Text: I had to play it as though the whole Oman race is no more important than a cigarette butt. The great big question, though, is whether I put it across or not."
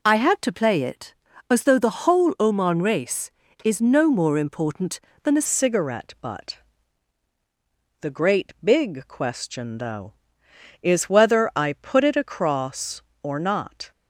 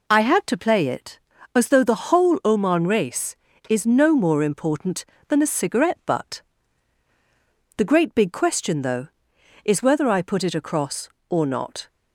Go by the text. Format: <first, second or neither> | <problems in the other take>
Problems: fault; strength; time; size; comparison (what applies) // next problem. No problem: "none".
second | changes voice at "cigarette"; from 5.4 s on; 8.5 s long